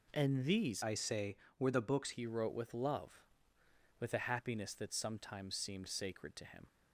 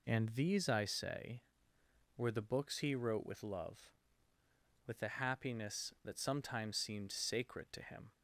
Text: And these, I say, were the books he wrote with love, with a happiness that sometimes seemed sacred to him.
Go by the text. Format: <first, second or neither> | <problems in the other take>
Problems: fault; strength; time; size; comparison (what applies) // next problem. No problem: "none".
second | changes voice from "I" to "books"; from 0.8 to 2.1 s; 1.3 s long